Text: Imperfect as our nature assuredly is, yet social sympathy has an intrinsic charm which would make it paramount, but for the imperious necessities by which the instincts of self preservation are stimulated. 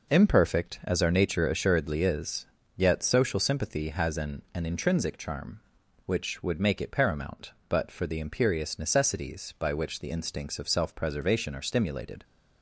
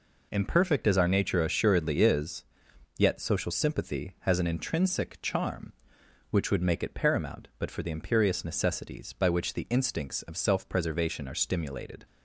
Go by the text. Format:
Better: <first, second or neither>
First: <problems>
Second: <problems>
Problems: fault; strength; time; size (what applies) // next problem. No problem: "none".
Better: second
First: says "an" twice; at 4.5 s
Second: none